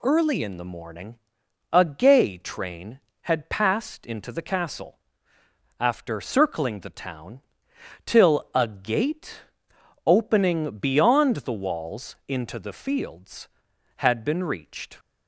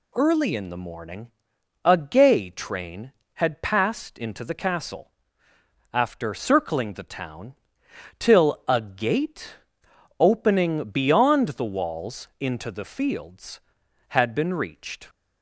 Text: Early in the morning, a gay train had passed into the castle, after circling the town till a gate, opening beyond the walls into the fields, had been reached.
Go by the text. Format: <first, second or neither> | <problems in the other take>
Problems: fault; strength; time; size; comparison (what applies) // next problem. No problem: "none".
neither | pauses between "town" and "till"; noticeable; the same in both